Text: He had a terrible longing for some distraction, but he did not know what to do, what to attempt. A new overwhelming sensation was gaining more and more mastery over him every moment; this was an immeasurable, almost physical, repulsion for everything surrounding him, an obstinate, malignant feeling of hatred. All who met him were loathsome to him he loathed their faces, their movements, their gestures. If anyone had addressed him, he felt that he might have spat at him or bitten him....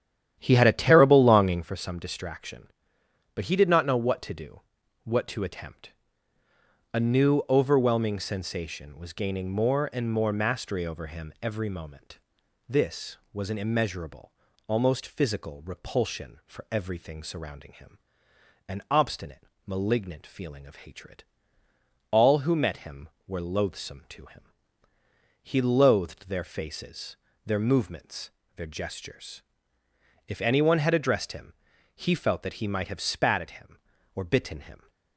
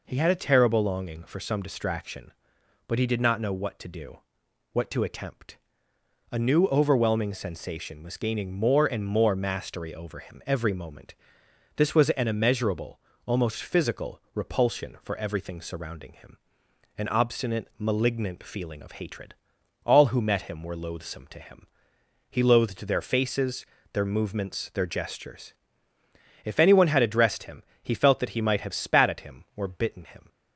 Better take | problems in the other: second | starts louder than the rest; strong; until 1.7 s; 10.5 dB // pauses between "him" and "he"; noticeable; at 24.4 s; 0.98 s long; noticeable in the second

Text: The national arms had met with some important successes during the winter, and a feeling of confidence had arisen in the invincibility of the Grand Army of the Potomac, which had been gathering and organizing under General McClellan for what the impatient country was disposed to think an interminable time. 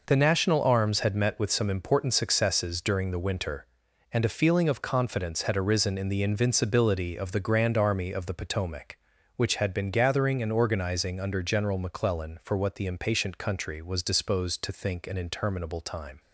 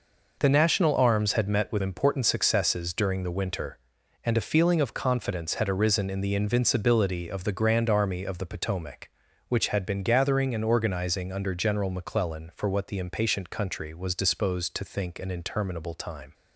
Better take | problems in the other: first | skips "some"; at 1.8 s

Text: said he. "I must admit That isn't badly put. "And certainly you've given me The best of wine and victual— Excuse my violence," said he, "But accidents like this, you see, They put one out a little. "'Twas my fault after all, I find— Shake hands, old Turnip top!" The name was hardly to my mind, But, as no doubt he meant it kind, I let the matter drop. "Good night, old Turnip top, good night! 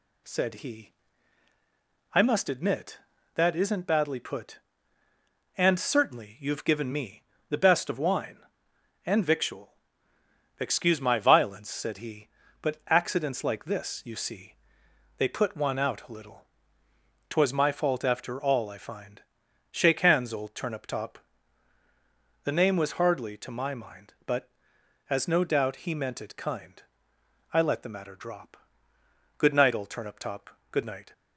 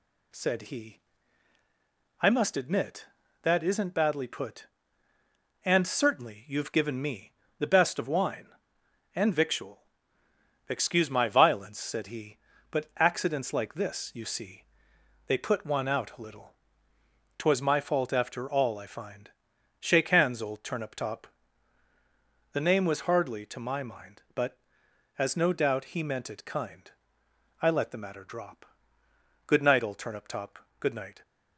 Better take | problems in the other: neither | pauses between "me" and "The"; slight; the same in both

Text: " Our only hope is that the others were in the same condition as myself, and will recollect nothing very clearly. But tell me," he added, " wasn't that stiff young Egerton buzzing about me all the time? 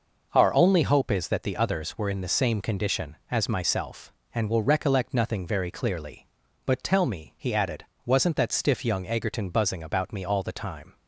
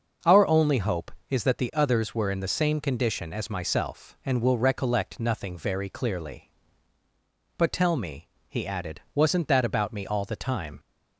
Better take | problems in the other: first | starts louder than the rest; until 1.4 s; 6 dB // skips "stiff young Egerton buzzing"; at 9.6 s

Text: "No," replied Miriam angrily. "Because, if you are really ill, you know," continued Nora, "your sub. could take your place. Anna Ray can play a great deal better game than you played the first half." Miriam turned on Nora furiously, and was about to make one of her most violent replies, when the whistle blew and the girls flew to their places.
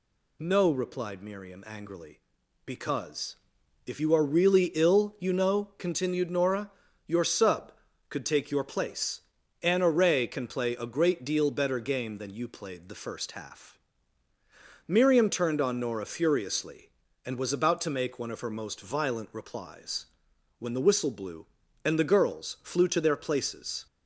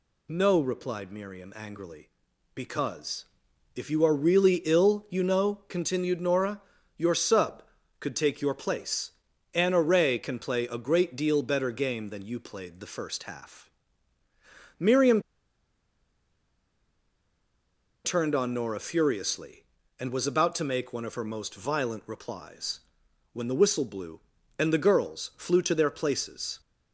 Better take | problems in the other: first | pauses between "Miriam" and "turned"; strong; at 15.1 s; 2.8 s long

